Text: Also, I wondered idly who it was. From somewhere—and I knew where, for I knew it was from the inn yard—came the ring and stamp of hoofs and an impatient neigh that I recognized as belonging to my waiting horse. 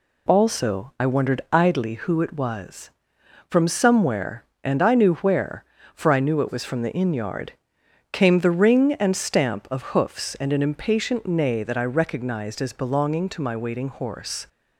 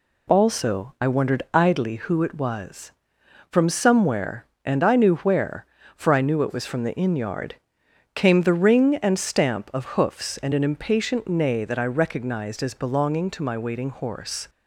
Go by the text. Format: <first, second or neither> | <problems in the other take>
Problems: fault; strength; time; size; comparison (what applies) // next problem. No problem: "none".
neither | none